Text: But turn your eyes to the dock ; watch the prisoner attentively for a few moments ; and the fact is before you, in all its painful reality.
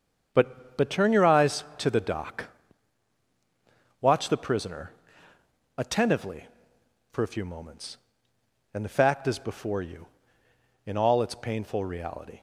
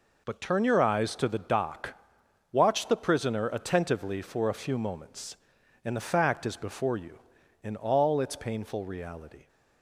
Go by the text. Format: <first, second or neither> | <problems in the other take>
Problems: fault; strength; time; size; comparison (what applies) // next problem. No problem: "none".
second | starts louder than the rest; until 1.3 s; 6 dB // says "But" twice; at 0.7 s // pauses between "prisoner" and "attentively"; noticeable; at 4.9 s; 0.84 s long